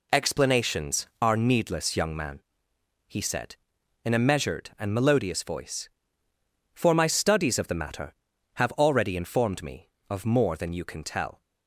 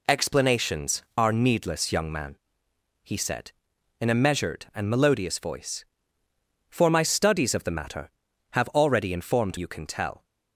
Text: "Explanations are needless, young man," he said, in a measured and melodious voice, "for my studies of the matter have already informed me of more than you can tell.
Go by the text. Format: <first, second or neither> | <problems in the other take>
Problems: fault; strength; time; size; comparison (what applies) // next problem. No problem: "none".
first | skips "me of more than"; at 9.5 s